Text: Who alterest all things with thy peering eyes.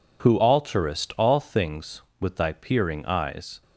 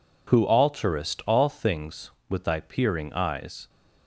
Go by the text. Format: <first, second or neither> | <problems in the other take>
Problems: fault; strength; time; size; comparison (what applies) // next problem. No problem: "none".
neither | none